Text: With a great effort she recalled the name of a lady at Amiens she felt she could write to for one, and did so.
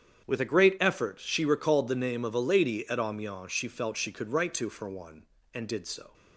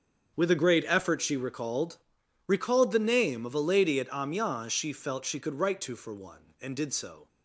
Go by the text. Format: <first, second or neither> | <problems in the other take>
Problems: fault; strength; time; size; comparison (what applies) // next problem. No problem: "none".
first | starts louder than the rest; strong; until 1.4 s; 7.5 dB; strong in the first // says "recalled" twice; at 2.4 s